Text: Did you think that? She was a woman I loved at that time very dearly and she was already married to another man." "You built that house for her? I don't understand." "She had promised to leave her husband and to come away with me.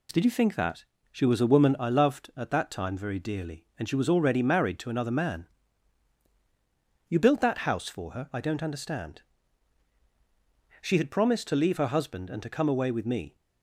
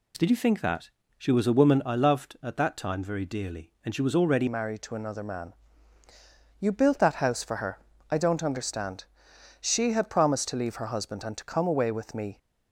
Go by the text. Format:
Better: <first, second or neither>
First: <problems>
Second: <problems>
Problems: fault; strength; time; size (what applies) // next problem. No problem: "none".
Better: first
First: none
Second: changes voice at "married"; from 4.4 s on; 7.9 s long